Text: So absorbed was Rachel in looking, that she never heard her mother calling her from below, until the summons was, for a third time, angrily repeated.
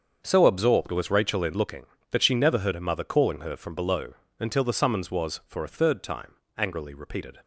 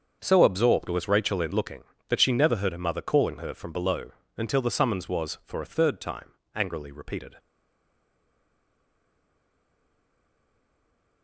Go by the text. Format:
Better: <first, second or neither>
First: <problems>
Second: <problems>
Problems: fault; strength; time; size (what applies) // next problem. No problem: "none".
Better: first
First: starts louder than the rest; until 1.2 s; 7 dB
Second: starts louder than the rest; until 1.2 s; 7 dB // stays silent after the last word; strong; from 7.3 s on; 3.9 s long